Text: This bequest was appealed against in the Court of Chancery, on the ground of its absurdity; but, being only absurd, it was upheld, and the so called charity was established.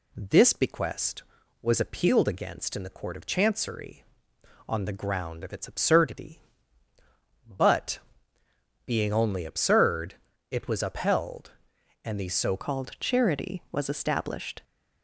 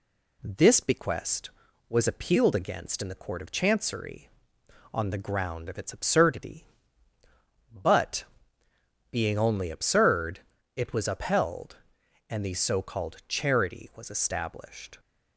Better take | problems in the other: second | changes voice at "called"; from 12.5 s on; 2.1 s long

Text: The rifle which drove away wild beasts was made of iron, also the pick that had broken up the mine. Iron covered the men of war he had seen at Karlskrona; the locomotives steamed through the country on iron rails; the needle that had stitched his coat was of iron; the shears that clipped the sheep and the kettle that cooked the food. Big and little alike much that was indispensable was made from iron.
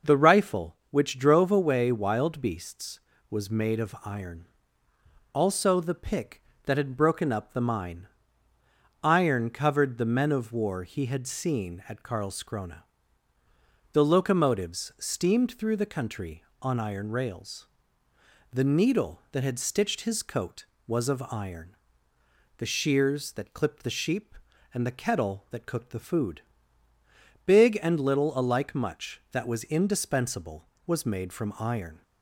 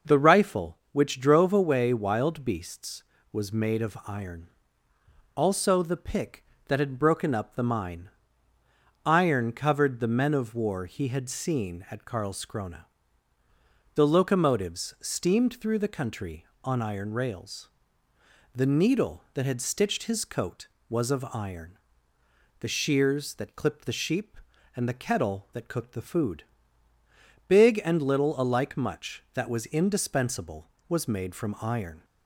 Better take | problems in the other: neither | none

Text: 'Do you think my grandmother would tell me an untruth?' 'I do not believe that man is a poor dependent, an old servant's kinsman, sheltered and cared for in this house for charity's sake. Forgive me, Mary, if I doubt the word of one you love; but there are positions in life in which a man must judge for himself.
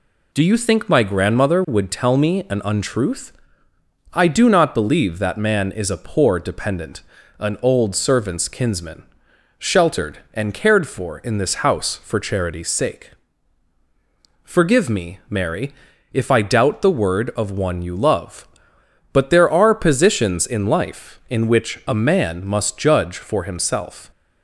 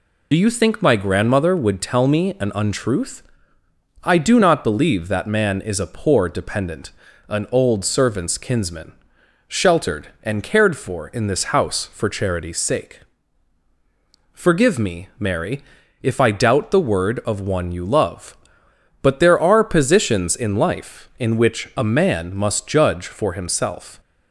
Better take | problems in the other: first | loses the start of "Do"; at 0.3 s; 45 ms

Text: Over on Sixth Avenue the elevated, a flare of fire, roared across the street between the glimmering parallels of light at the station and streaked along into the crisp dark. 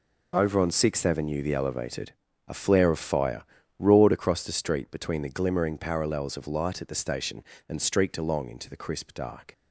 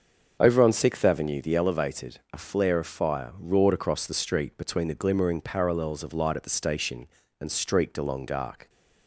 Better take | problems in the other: first | starts louder than the rest; until 1.4 s; 6.5 dB // skips "into the crisp"; at 8.2 s

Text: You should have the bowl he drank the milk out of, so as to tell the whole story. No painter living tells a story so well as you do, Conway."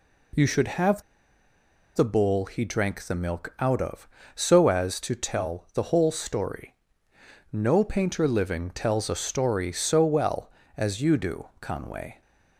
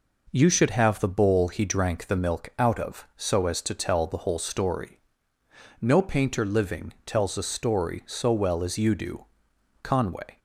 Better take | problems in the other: second | pauses between "have" and "the"; noticeable; at 1.0 s; 0.93 s long

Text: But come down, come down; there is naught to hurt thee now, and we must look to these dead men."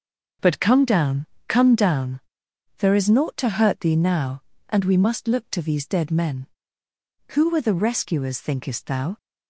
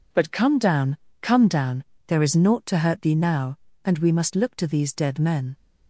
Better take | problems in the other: second | starts louder than the rest; until 1.6 s; 6.5 dB // goes on to say "Who were the rescuers thinkest thou"; strong; from 7.3 s on; 1.8 s long

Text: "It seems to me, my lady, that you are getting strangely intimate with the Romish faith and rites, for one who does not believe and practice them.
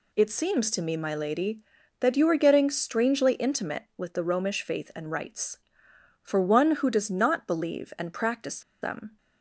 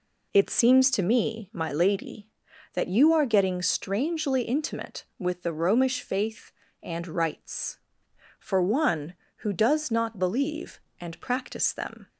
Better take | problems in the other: second | pauses between "practice" and "them"; slight; at 8.6 s; 0.21 s long

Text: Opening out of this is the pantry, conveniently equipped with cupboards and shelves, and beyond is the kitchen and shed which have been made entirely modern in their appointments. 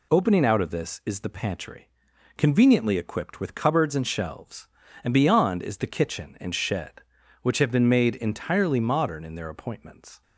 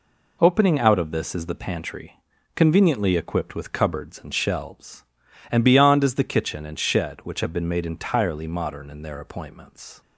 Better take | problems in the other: neither | none

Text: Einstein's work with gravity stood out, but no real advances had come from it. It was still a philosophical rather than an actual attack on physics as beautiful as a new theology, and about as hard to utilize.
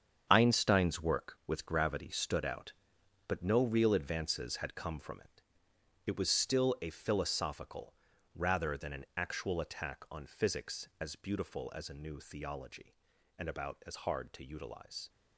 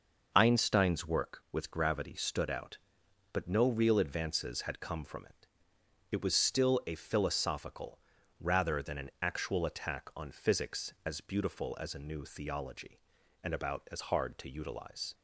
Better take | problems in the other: second | gets quieter; strong; throughout; 10 dB // pauses between "philosophical" and "rather"; at 7.9 s; 0.40 s long; also in the second

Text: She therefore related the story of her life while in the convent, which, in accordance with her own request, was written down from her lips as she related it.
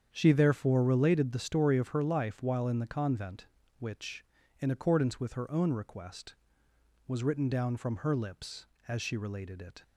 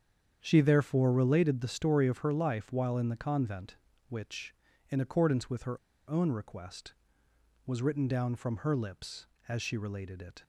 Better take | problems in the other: first | starts louder than the rest; strong; until 1.4 s; 8 dB; strong in the first // pauses between "her" and "own"; slight; at 5.7 s; 0.33 s long

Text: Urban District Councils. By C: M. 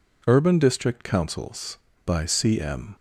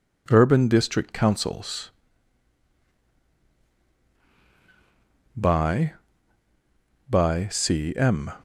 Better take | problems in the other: first | says "By" twice; at 7.0 s

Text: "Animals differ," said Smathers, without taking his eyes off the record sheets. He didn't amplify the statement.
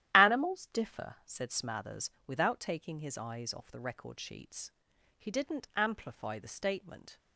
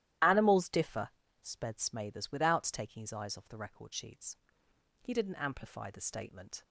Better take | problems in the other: first | starts louder than the rest; strong; until 1.5 s; 13 dB; strong in the first // says "sped" for "said"; at 1.4 s

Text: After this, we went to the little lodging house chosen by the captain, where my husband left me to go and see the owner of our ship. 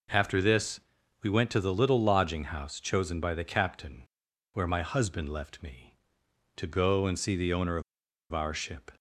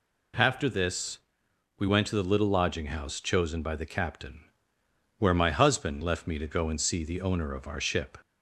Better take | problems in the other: second | pauses between "of" and "our"; noticeable; at 7.8 s; 0.50 s long

